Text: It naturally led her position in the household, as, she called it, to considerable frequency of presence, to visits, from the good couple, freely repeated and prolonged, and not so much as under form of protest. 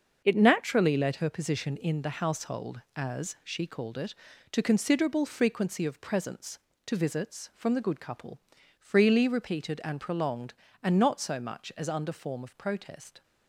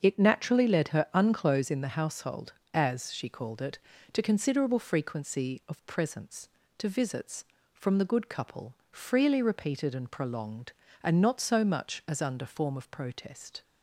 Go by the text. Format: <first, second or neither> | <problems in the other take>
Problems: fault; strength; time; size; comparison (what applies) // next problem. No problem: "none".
first | starts louder than the rest; until 1.0 s; 7 dB; also in the first // says "unclose" for "position"; at 1.1 s